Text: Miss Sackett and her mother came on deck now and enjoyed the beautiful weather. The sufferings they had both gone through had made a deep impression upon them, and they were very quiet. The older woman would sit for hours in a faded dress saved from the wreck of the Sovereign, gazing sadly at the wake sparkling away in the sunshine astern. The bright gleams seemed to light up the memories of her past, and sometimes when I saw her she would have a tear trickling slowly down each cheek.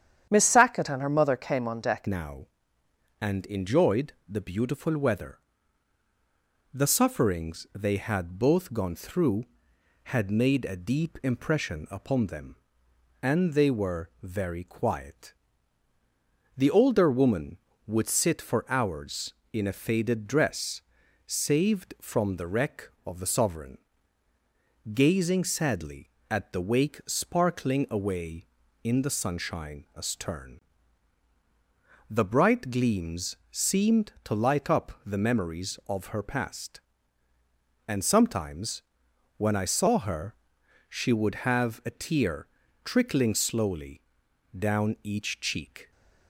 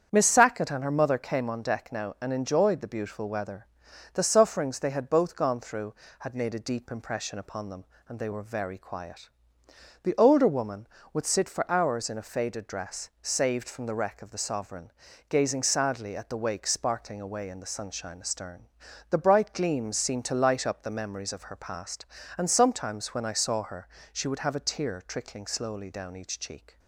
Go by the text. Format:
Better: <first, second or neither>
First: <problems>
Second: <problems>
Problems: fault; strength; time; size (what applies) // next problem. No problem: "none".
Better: second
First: starts louder than the rest; strong; until 1.3 s; 9.5 dB // changes voice at "now"; from 2.0 s on; 43.9 s long // pauses between "dress" and "saved"; noticeable; at 20.8 s; 0.46 s long // pauses between "sometimes" and "when"; noticeable; at 38.8 s; 0.54 s long // pauses between "her" and "she"; noticeable; at 40.3 s; 0.54 s long // pauses between "tear" and "trickling"; slight; at 42.4 s; 0.36 s long // pauses between "slowly" and "down"; noticeable; at 44.0 s; 0.56 s long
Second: starts louder than the rest; strong; until 1.1 s; 8 dB // pauses between "her" and "she"; slight; at 23.8 s; 0.24 s long